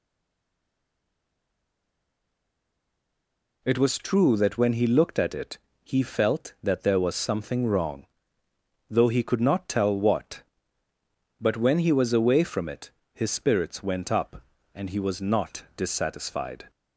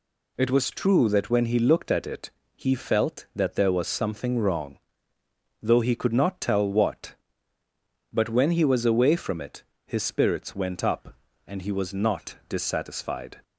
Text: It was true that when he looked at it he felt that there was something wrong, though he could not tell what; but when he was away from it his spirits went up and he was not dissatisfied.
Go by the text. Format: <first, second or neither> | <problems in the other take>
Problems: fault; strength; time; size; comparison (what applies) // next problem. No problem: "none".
second | stays silent before the first word; strong; until 3.6 s; 3.6 s long // pauses between "it" and "he"; slight; at 5.5 s; 0.26 s long; slight in the second // pauses between "it" and "his"; slight; at 12.8 s; 0.22 s long; slight in the second